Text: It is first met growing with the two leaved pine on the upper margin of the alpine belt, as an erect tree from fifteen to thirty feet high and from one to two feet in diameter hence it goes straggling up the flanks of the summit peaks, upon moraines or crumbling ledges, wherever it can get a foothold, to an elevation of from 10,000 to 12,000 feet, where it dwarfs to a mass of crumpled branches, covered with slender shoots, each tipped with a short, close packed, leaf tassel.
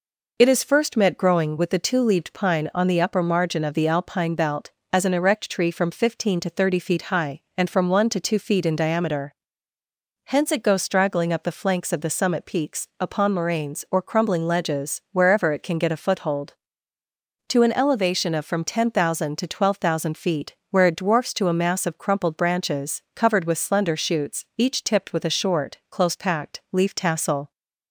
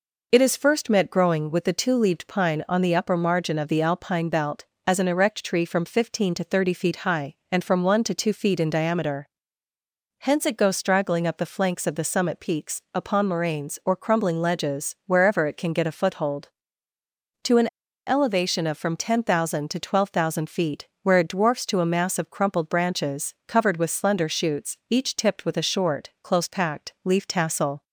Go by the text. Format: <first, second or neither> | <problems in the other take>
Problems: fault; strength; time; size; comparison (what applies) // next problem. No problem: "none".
first | pauses between "diameter" and "hence"; noticeable; at 9.2 s; 0.92 s long; noticeable in the first // pauses between "an" and "elevation"; at 17.6 s; 0.40 s long